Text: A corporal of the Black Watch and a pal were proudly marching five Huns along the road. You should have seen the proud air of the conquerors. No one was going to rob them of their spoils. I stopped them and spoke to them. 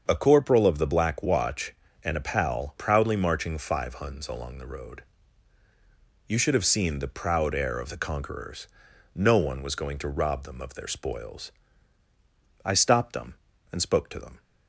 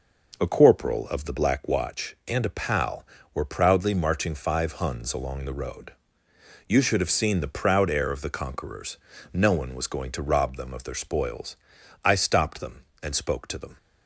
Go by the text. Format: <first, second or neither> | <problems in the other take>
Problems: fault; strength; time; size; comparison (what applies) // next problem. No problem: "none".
second | starts louder than the rest; until 1.0 s; 7 dB // skips "were"; at 2.7 s